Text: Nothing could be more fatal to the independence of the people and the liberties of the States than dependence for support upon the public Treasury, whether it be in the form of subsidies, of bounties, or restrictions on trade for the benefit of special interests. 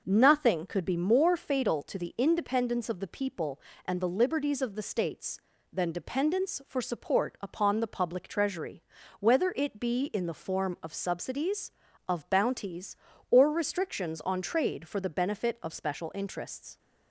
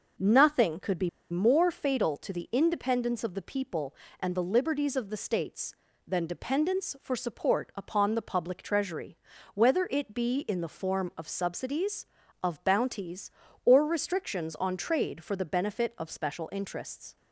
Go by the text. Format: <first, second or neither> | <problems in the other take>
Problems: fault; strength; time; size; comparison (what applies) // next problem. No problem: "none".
first | pauses between "be" and "more"; slight; at 1.0 s; 0.22 s long